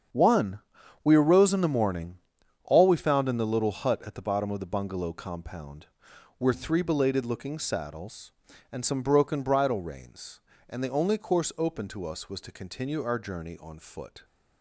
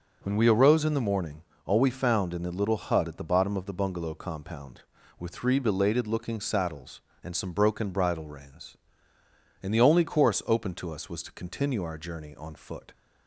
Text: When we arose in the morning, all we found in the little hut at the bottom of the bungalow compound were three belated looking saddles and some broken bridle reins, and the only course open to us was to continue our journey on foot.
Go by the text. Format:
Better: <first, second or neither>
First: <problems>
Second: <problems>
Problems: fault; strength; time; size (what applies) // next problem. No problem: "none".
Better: second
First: starts louder than the rest; strong; until 1.5 s; 7.5 dB // says "One" for "When"; at 0.1 s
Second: none